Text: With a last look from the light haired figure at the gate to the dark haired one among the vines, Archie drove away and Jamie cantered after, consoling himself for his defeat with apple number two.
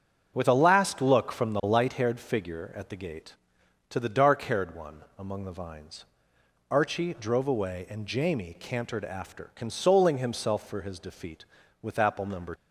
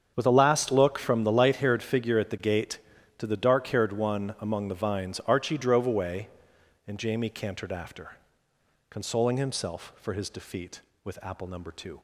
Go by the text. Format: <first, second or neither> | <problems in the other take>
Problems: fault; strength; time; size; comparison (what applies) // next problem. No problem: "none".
second | starts louder than the rest; strong; until 1.3 s; 8 dB; strong in the second // stops before "two"; at 12.5 s